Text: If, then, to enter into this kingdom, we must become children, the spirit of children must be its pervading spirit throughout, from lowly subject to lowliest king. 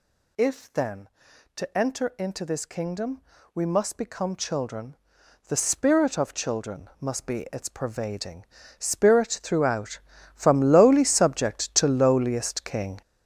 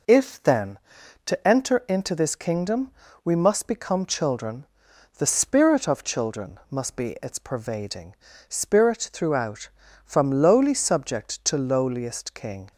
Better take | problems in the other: second | gets louder; strong; throughout; 8.5 dB // pauses between "pervading" and "spirit"; slight; at 8.4 s; 0.34 s long; slight in the second

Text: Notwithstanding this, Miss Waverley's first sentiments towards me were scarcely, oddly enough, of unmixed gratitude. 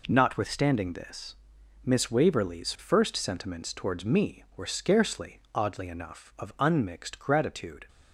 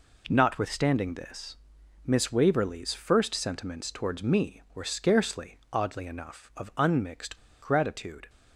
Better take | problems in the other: first | pauses between "unmixed" and "gratitude"; slight; at 7.3 s; 0.23 s long

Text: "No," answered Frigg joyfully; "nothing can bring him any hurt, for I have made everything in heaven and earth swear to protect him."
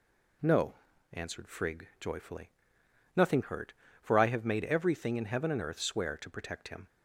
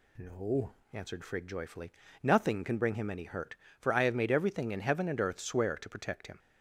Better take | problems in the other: second | skips "can bring him any"; at 3.4 s

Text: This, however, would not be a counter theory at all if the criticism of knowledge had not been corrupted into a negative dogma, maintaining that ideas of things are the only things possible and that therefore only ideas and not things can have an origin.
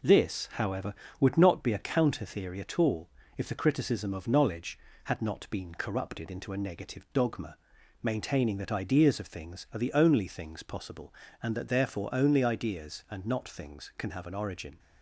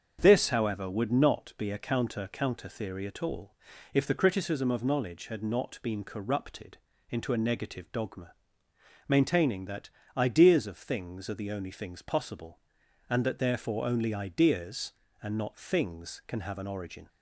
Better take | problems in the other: first | starts louder than the rest; until 1.2 s; 7 dB // says "counter" twice; at 2.3 s // pauses between "all" and "if"; at 3.5 s; 0.40 s long; slight in the first // pauses between "corrupted" and "into"; slight; at 6.7 s; 0.32 s long // pauses between "that" and "ideas"; slight; at 9.8 s; 0.28 s long

